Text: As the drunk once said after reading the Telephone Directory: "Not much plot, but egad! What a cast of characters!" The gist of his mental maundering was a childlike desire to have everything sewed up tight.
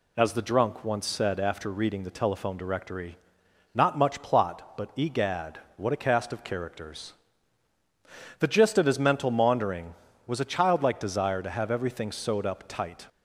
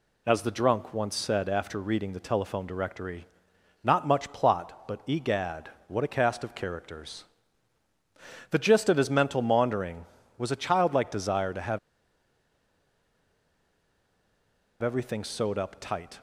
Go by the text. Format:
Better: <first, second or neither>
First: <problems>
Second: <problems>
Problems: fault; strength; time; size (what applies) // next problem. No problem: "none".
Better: first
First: none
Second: pauses between "have" and "everything"; strong; at 11.7 s; 3.0 s long